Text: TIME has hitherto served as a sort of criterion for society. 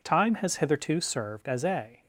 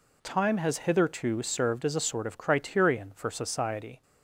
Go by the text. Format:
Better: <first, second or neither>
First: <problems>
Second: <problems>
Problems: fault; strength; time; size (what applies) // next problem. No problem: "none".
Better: second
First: stops before "sort of criterion for society"; at 2.0 s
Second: none